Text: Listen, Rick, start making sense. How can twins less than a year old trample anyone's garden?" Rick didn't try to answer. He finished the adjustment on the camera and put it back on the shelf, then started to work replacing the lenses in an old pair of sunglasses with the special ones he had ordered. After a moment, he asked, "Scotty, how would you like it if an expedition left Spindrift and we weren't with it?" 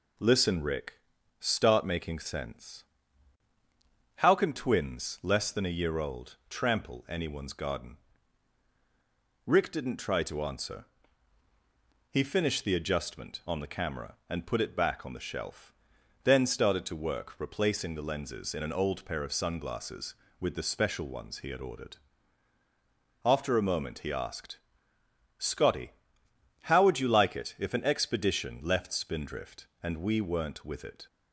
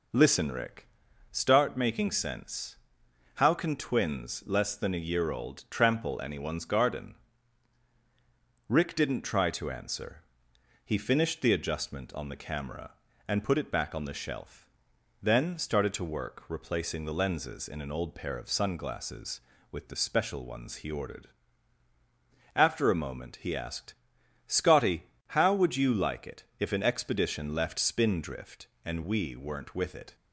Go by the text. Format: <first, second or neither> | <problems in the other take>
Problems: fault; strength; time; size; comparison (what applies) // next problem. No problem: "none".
first | skips "had"; at 20.8 s